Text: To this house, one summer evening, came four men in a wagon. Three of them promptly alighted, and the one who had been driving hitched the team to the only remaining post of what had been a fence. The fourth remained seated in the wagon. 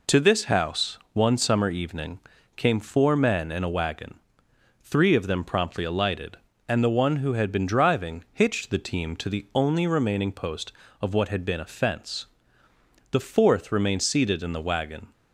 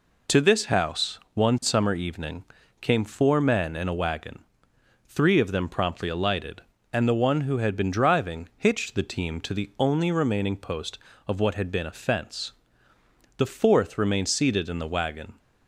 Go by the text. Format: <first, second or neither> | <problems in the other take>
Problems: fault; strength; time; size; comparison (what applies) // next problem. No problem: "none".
neither | none